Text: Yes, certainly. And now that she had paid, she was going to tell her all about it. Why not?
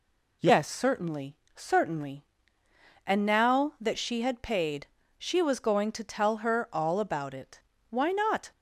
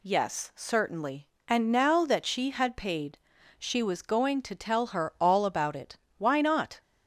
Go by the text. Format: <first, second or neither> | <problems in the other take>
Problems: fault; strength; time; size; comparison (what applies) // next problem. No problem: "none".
second | says "certainly" twice; at 1.5 s